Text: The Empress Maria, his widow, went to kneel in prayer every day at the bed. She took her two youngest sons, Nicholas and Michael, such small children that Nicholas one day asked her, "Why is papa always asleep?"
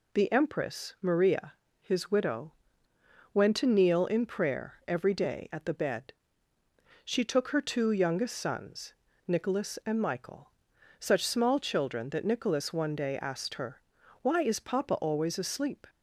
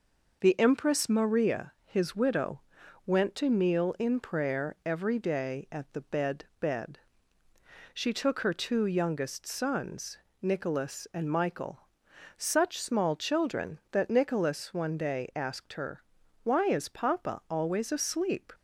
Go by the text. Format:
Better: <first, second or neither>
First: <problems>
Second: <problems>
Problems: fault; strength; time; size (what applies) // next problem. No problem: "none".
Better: first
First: none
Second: says "bed" twice; at 6.5 s